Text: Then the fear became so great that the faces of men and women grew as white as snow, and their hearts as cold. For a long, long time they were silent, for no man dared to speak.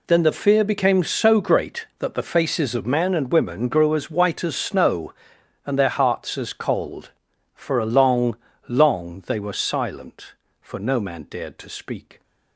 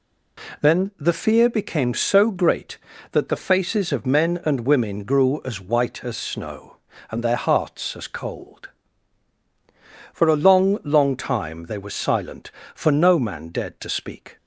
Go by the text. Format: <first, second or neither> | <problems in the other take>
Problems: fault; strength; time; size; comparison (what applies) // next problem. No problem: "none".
second | skips "time"; at 9.2 s